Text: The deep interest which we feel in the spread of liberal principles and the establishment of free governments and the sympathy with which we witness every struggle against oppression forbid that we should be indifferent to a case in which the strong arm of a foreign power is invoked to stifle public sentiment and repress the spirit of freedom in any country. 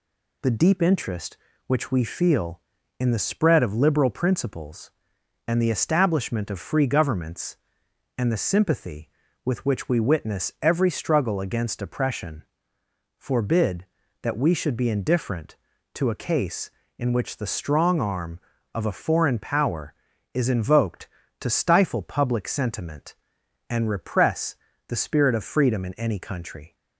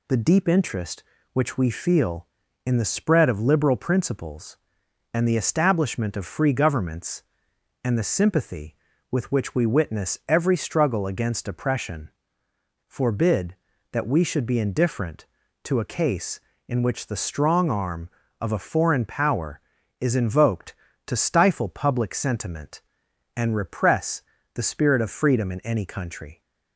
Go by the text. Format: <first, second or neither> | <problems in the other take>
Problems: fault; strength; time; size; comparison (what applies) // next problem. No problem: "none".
neither | pauses between "oppression" and "forbid"; noticeable; the same in both // pauses between "repress" and "the"; slight; the same in both